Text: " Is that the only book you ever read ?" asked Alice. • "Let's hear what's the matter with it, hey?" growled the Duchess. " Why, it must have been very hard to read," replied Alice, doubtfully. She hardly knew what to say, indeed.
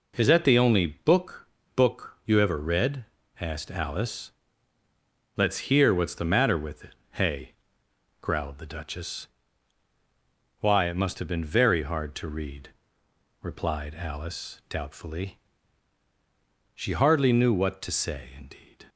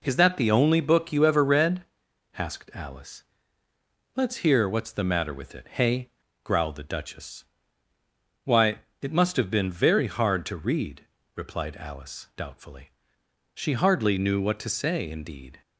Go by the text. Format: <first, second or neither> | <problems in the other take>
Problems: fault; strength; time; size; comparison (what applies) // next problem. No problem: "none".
second | says "book" twice; at 1.7 s